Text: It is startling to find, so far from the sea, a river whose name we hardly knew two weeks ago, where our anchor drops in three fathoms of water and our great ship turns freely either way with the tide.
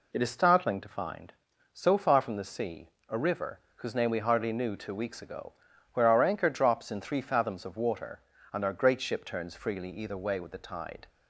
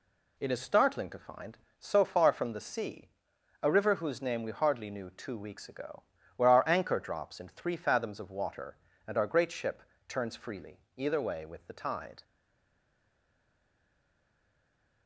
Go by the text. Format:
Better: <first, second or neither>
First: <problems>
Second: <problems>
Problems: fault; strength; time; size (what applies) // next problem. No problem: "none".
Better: first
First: none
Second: pauses between "ship" and "turns"; slight; at 9.8 s; 0.26 s long // pauses between "freely" and "either"; slight; at 10.7 s; 0.16 s long // stays silent after the last word; strong; from 12.2 s on; 2.8 s long